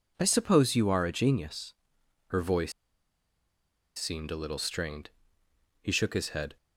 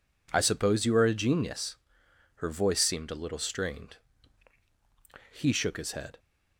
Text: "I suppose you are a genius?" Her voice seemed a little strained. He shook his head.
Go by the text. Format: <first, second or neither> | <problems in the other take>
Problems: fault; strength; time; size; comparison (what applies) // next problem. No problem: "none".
second | pauses between "voice" and "seemed"; at 2.7 s; 1.2 s long